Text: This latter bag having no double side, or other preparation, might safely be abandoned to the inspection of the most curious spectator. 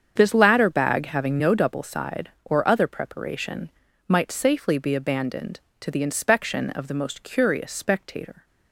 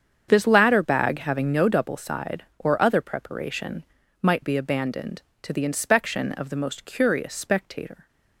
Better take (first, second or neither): first